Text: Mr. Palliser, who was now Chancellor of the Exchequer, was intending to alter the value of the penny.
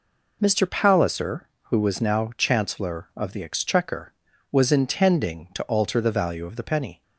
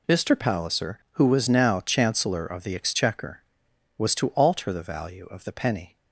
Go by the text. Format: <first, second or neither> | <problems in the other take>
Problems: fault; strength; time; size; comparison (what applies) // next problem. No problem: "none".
first | skips "intending"; at 4.1 s